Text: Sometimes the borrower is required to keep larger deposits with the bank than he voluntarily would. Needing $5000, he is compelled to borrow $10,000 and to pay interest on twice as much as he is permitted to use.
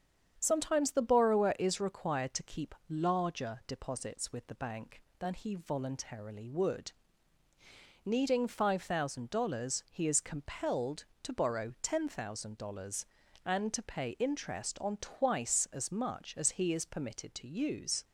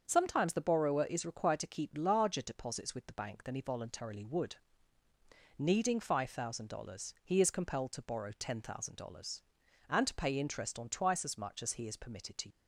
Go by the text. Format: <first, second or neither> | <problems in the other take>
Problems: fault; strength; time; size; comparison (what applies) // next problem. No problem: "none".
first | starts louder than the rest; until 1.0 s; 7 dB; strong in the first // stops before "use"; at 12.4 s